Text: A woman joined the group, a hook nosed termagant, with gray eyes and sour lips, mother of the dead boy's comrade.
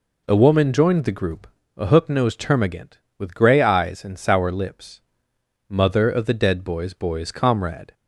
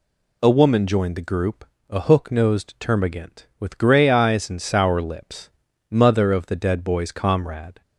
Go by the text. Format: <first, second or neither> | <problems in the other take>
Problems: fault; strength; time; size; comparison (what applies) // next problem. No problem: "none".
second | says "boy's" twice; at 6.9 s